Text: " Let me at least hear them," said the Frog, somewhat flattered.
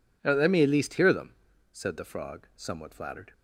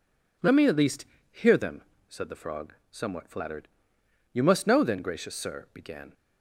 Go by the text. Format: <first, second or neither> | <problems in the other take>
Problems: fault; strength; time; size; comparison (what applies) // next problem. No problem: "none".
first | pauses between "least" and "hear"; slight; at 1.0 s; 0.28 s long // goes on to say "You must know then gracious Sir began"; strong; from 4.3 s on; 1.8 s long